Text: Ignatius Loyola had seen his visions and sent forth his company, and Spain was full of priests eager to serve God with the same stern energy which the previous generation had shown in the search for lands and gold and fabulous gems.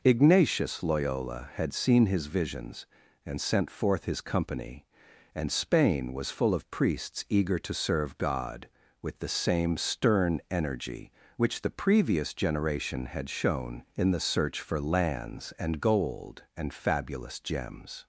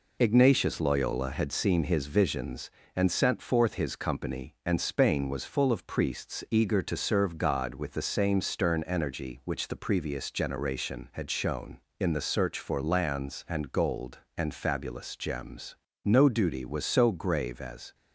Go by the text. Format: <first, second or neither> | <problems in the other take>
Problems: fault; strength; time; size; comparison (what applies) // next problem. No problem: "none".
first | goes on to say "No duty was so grave as"; strong; from 16.0 s on; 1.9 s long